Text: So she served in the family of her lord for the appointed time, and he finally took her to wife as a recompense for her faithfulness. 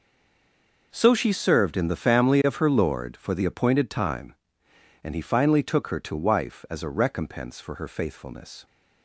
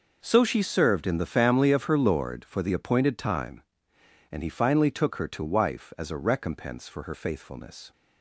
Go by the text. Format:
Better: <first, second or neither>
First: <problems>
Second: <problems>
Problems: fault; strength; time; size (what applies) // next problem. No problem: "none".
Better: second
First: stays silent before the first word; slight; until 0.9 s; 0.9 s long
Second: none